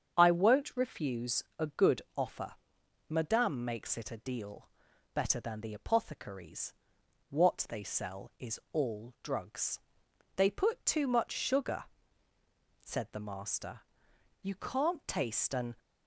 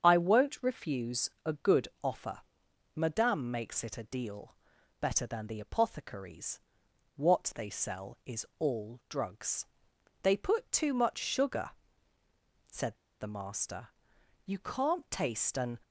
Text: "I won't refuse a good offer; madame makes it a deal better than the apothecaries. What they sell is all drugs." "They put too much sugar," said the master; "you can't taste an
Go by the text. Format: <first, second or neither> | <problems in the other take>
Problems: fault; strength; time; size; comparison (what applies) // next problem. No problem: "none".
first | starts louder than the rest; strong; until 1.0 s; 7.5 dB; strong in the first // pauses between "refuse" and "a"; slight; at 1.2 s; 0.16 s long; slight in the first // pauses between "good" and "offer"; slight; at 1.8 s; 0.16 s long; slight in the first // pauses between "deal" and "better"; noticeable; at 4.5 s; 0.46 s long; noticeable in the first // pauses between "said" and "the"; slight; at 12.9 s; 0.23 s long